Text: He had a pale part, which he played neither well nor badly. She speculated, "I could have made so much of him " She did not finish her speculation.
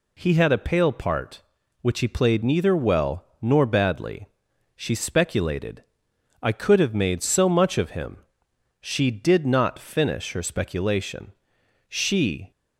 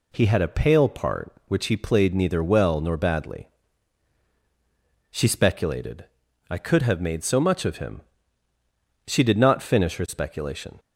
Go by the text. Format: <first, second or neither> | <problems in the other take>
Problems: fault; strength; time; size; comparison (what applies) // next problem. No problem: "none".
second | pauses between "well" and "nor"; slight; at 3.2 s; 0.18 s long // goes on to say "She"; noticeable; from 11.8 s on; 0.64 s long